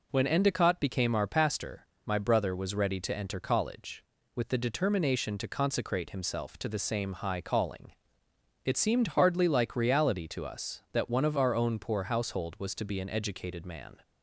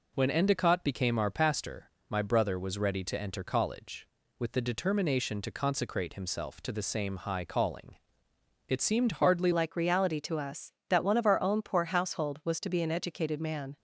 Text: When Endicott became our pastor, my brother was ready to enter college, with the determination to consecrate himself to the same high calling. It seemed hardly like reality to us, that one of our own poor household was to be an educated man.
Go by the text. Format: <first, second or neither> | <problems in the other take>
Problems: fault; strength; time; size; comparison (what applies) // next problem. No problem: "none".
first | changes voice at "like"; from 9.5 s on; 4.2 s long